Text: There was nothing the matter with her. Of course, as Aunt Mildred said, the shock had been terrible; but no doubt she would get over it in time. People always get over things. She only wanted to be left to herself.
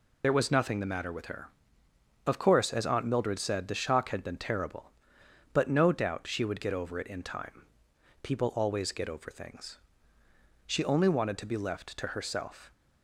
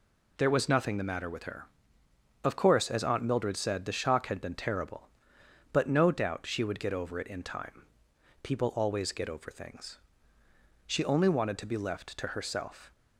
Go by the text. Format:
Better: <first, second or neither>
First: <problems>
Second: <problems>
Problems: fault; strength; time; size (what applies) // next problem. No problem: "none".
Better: second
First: loses the start of "There"; at 0.2 s; 45 ms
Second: none